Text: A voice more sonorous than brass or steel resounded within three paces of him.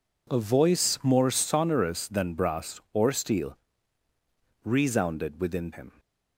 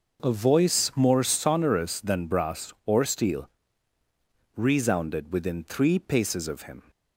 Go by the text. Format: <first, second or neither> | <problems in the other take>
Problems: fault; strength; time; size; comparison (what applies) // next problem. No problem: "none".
second | pauses between "steel" and "resounded"; at 3.5 s; 1.0 s long; also in the second // skips "three paces of"; at 5.7 s